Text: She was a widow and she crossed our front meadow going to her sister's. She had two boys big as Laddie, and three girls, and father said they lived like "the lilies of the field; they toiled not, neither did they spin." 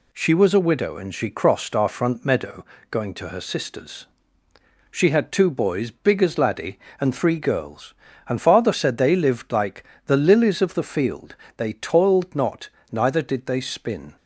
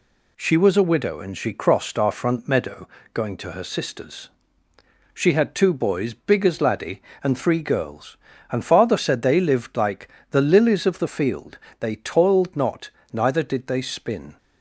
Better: neither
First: pauses between "meadow" and "going"; slight; at 2.6 s; 0.24 s long // pauses between "like" and "the"; slight; at 9.8 s; 0.22 s long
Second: pauses between "meadow" and "going"; slight; at 2.8 s; 0.24 s long // pauses between "like" and "the"; slight; at 10.0 s; 0.22 s long

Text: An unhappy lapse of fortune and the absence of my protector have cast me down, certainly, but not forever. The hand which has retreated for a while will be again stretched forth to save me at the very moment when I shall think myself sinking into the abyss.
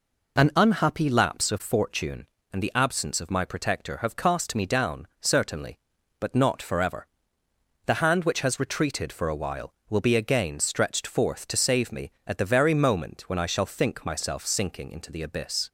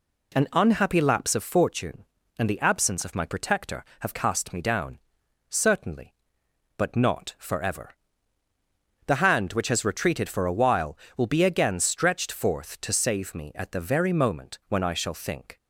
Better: first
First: none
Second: stops before "myself sinking into the abyss"; at 15.5 s

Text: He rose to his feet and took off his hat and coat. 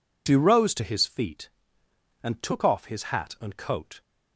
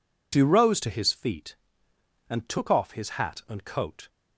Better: neither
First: none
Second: none

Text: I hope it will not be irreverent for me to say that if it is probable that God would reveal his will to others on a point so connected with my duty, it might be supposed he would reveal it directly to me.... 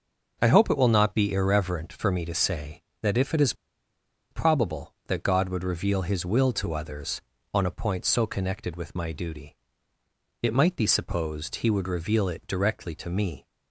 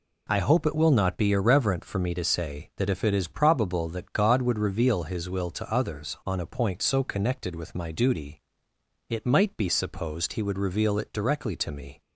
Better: second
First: pauses between "is" and "probable"; noticeable; at 3.5 s; 0.77 s long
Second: none

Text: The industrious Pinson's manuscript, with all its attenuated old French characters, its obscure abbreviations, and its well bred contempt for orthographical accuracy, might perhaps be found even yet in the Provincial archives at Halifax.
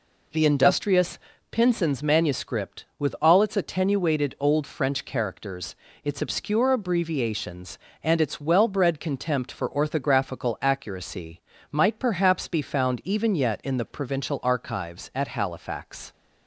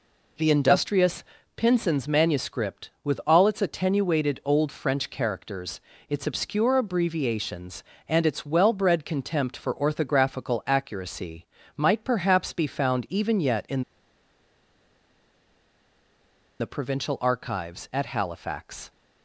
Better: first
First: pauses between "industrious" and "Pinson's"; slight; at 1.1 s; 0.32 s long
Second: pauses between "industrious" and "Pinson's"; slight; at 1.2 s; 0.32 s long // pauses between "in" and "the"; strong; at 13.8 s; 2.7 s long

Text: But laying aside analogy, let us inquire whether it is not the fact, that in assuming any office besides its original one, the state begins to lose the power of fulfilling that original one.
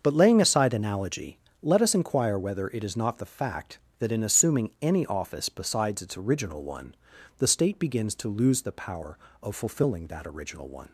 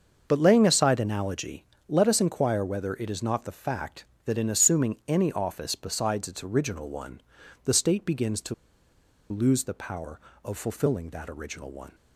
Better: first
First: starts louder than the rest; until 1.0 s; 6.5 dB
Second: starts louder than the rest; until 1.2 s; 6.5 dB // pauses between "to" and "lose"; noticeable; at 8.5 s; 0.76 s long

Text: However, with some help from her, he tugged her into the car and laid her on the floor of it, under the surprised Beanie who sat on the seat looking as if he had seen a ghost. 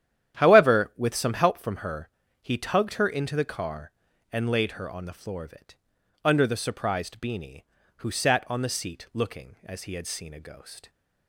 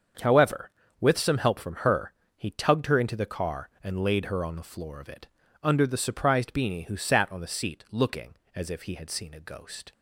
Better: second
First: starts louder than the rest; strong; until 1.4 s; 10.5 dB // skips "if"; at 9.8 s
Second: starts louder than the rest; until 1.5 s; 7 dB

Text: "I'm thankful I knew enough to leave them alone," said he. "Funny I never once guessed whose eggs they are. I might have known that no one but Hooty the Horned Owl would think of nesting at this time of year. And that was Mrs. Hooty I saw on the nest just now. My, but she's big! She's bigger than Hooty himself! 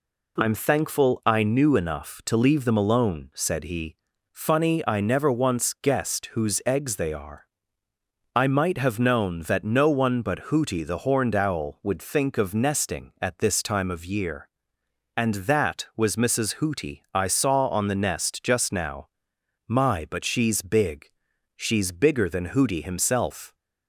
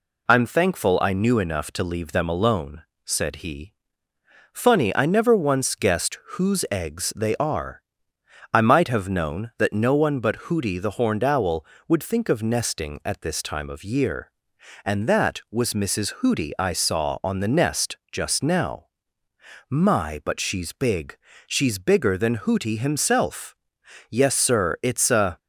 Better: first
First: none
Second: pauses between "guessed" and "whose"; slight; at 6.1 s; 0.18 s long // goes on to say "Yes Sir it's a"; noticeable; from 24.0 s on; 1.2 s long

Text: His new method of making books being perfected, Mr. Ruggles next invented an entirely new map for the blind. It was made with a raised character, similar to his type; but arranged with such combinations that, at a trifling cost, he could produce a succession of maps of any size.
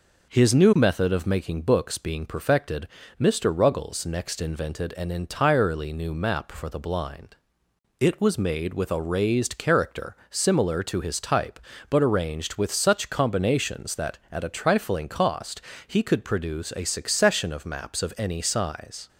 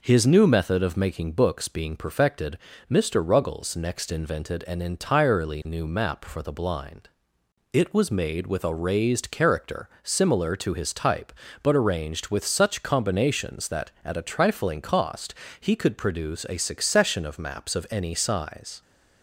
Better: neither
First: none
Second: none

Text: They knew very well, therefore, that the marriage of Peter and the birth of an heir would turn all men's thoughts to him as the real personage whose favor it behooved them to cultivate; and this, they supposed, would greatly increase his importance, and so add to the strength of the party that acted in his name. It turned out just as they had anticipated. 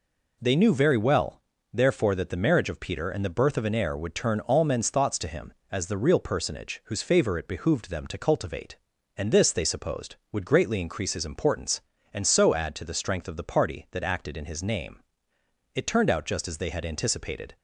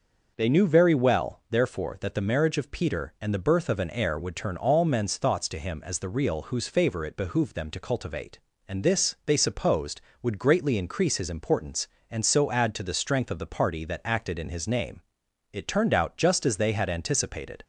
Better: first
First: none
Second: starts louder than the rest; noticeable; until 1.3 s; 6 dB // skips "personage"; at 6.4 s

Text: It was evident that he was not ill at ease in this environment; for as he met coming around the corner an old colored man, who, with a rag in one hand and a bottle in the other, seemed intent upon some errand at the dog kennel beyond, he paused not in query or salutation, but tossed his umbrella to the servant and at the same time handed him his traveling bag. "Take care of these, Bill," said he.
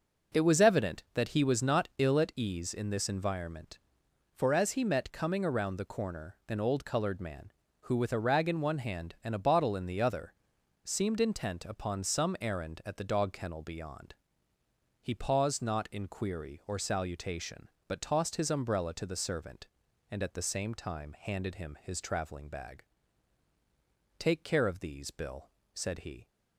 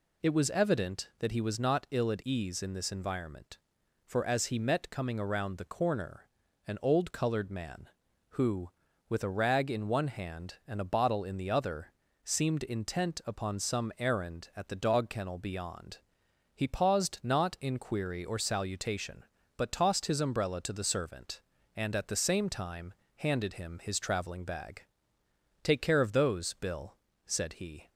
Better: first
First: none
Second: pauses between "corner" and "an"; at 6.2 s; 0.40 s long // pauses between "time" and "handed"; slight; at 22.9 s; 0.22 s long // says "those" for "these"; at 26.1 s

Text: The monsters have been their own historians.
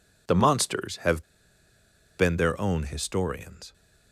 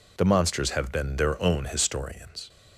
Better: second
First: pauses between "have" and "been"; noticeable; at 1.2 s; 0.97 s long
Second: none

